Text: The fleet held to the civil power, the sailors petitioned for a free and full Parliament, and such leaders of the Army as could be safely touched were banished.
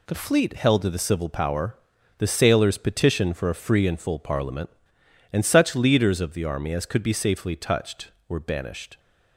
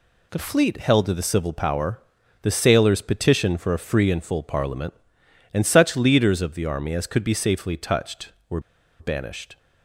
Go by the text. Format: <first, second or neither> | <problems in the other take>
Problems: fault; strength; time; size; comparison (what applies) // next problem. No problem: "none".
first | pauses between "were" and "banished"; at 8.5 s; 0.40 s long